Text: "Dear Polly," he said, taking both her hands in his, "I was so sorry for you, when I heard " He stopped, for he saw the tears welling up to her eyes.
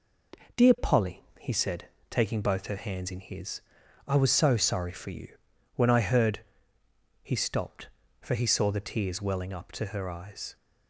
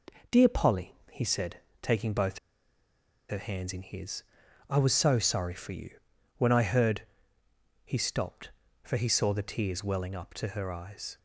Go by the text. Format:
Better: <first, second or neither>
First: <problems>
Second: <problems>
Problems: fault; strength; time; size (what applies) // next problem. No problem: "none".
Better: first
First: none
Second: pauses between "both" and "her"; noticeable; at 2.3 s; 0.91 s long